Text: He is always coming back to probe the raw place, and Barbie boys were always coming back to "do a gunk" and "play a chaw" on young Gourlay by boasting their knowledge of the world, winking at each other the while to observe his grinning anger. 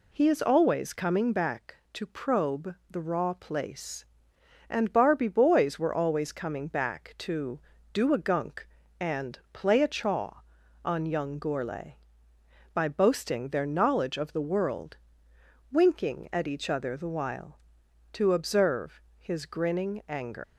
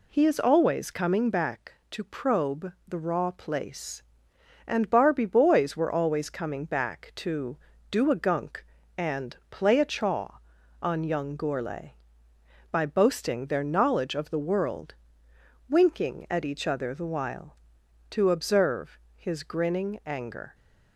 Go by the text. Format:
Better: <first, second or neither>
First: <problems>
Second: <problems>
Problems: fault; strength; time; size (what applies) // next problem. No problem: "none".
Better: second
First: pauses between "observe" and "his"; slight; at 18.9 s; 0.18 s long // leaves "anger" unfinished; at 20.4 s; 130 ms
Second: pauses between "observe" and "his"; slight; at 18.9 s; 0.18 s long